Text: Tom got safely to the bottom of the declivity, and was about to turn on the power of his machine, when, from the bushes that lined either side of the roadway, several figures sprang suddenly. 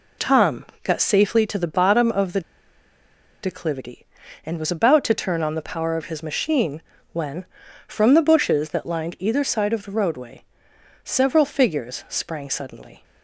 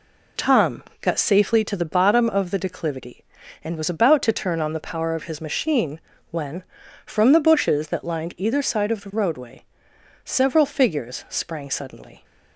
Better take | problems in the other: second | pauses between "Tom" and "got"; slight; at 0.6 s; 0.18 s long; slight in the second // pauses between "the" and "declivity"; at 2.4 s; 1.0 s long

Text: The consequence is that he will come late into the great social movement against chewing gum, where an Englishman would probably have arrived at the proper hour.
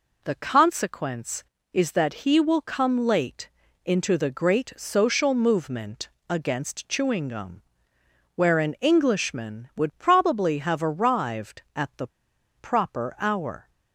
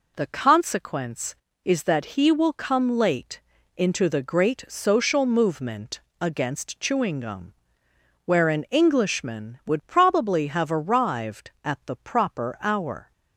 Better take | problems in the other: second | pauses between "late" and "into"; slight; at 3.4 s; 0.36 s long; slight in the second // pauses between "movement" and "against"; slight; at 6.0 s; 0.20 s long; slight in the second // pauses between "the" and "proper"; noticeable; at 12.0 s; 0.49 s long

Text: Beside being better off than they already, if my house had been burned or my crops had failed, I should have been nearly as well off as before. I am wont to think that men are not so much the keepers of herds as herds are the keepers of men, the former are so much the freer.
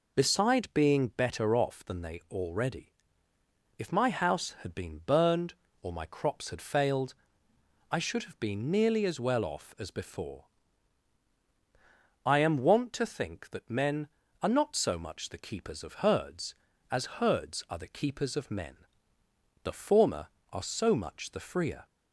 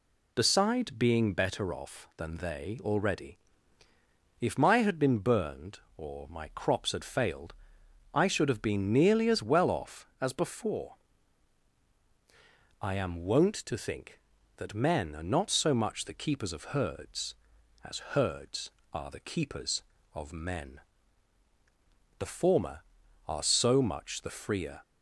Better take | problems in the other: first | skips "house"; at 4.7 s

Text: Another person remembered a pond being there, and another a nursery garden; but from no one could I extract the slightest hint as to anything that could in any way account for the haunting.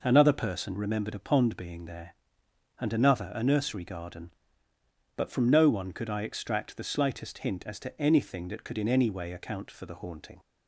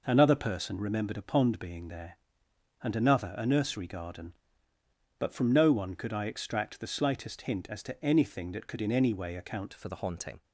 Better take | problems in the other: first | changes voice at "for"; from 9.7 s on; 0.7 s long

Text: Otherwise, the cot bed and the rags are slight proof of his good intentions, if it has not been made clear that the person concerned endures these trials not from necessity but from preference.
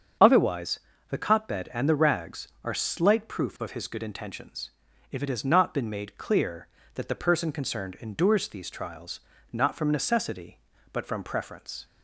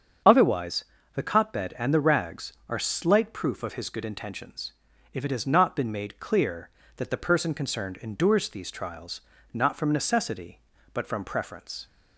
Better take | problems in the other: neither | starts louder than the rest; strong; the same in both // pauses between "trials" and "not"; slight; the same in both

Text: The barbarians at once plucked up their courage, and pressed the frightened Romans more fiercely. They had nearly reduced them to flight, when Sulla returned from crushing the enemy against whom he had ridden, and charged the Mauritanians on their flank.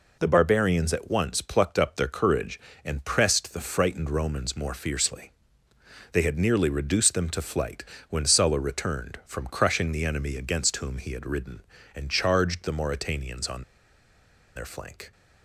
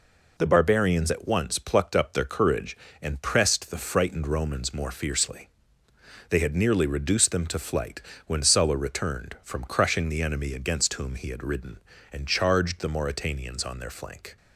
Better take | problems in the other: second | pauses between "on" and "their"; noticeable; at 13.6 s; 0.93 s long

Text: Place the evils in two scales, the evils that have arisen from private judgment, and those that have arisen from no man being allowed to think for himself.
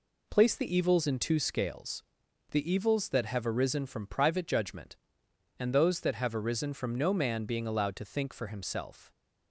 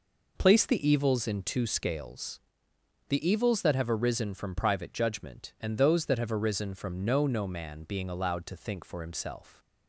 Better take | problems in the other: first | says "no" twice; at 7.2 s

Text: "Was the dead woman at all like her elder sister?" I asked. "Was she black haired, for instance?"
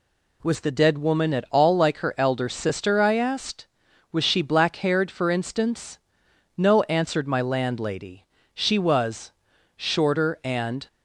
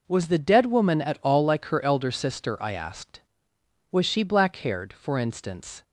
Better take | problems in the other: second | goes on to say "No answered my landlady she was shorter and"; strong; from 6.5 s on; 4.3 s long

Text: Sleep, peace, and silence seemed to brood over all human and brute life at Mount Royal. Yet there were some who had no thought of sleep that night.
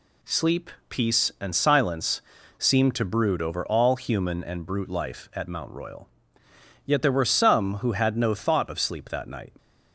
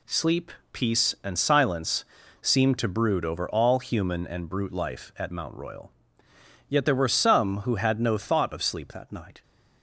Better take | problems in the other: first | pauses between "silence" and "seemed"; at 2.0 s; 0.38 s long; also in the first // changes voice at "that"; from 8.9 s on; 0.5 s long

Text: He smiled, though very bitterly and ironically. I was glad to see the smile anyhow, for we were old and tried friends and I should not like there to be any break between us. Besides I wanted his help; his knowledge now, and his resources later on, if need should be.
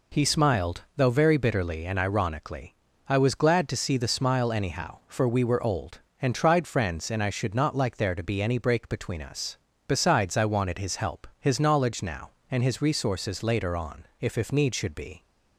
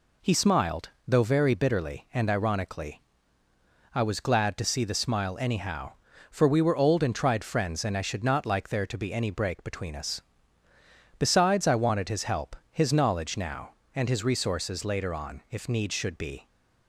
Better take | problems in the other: second | says "if" twice; at 14.3 s

